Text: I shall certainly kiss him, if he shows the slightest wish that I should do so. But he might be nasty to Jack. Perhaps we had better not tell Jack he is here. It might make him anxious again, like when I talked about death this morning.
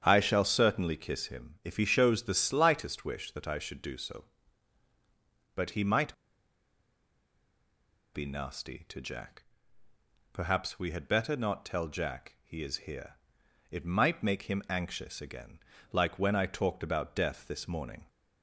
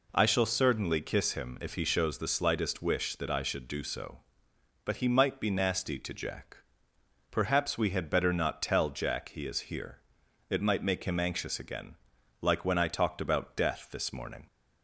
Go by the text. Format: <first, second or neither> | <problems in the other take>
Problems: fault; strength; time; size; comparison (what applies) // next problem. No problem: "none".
second | starts louder than the rest; strong; until 1.0 s; 8.5 dB // pauses between "might" and "be"; strong; at 6.1 s; 2.0 s long